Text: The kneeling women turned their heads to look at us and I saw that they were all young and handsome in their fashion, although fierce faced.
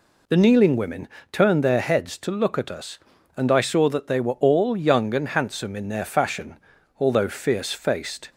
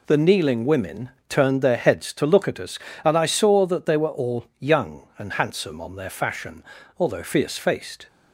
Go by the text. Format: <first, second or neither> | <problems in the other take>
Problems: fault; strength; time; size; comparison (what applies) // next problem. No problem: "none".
first | pauses between "women" and "turned"; slight; at 1.0 s; 0.20 s long; slight in the first // says "on" for "in"; at 5.8 s